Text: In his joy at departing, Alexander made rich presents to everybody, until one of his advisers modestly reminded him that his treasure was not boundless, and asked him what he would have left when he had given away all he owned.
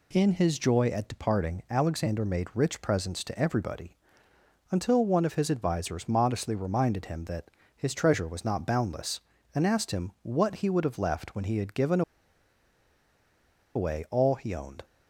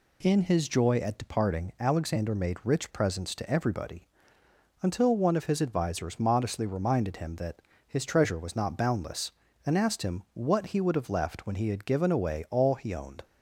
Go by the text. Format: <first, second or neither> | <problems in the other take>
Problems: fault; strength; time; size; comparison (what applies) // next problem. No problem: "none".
second | pauses between "that" and "his"; slight; at 7.4 s; 0.28 s long; slight in the second // pauses between "given" and "away"; strong; at 12.0 s; 1.7 s long